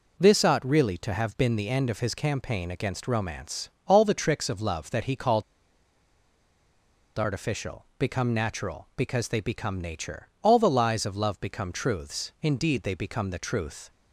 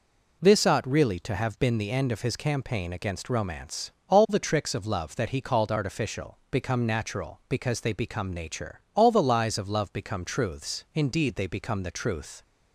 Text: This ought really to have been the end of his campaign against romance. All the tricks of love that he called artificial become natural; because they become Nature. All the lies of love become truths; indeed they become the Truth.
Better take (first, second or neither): second